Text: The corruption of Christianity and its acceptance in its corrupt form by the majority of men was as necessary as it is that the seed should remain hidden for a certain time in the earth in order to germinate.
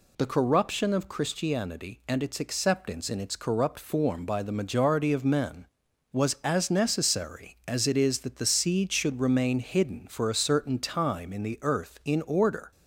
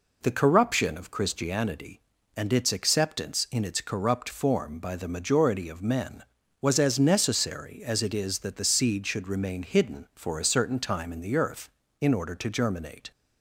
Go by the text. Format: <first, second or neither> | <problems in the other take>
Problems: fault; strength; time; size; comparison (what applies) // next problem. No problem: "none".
second | stops before "to germinate"; at 12.7 s